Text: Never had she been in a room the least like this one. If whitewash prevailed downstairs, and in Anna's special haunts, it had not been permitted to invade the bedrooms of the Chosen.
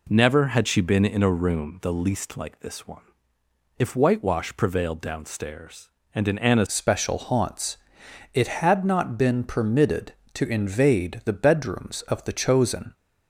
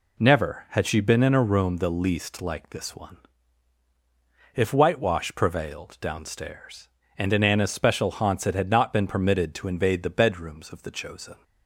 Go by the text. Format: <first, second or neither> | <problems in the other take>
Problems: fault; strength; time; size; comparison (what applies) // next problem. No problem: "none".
second | changes voice at "special"; from 6.6 s on; 6.3 s long